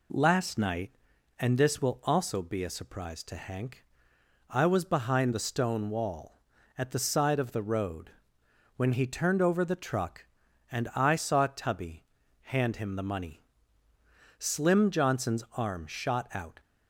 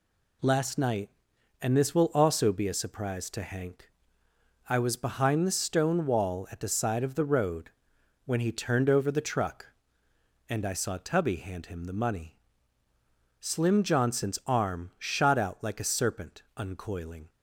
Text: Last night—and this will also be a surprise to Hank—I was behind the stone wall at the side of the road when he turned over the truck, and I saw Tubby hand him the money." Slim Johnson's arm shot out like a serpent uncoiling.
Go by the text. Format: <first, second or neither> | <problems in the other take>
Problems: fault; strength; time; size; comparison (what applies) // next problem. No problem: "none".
second | pauses between "road" and "when"; noticeable; at 8.0 s; 0.66 s long; noticeable in the second // pauses between "Tubby" and "hand"; slight; at 12.0 s; 0.36 s long // stops before "like a serpent uncoiling"; at 16.5 s